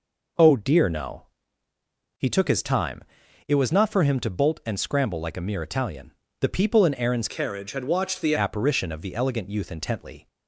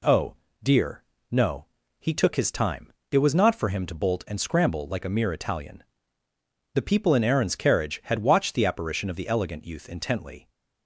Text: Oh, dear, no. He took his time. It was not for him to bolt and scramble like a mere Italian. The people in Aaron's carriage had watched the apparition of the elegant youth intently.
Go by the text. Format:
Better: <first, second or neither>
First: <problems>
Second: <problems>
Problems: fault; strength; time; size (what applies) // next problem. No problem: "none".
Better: second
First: changes voice from "carriage" to "the"; from 7.2 to 8.3 s; 1.1 s long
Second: none